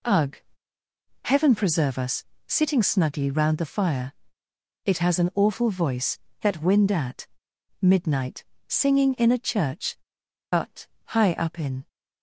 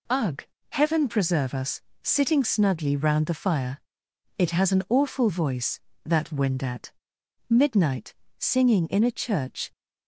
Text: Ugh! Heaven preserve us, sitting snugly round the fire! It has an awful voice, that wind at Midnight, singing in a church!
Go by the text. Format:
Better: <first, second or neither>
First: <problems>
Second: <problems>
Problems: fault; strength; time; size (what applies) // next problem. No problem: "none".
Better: second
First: pauses between "at" and "Midnight"; noticeable; at 7.2 s; 0.54 s long // goes on to say "But high up in"; from 10.5 s on; 1.3 s long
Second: pauses between "at" and "Midnight"; noticeable; at 6.9 s; 0.58 s long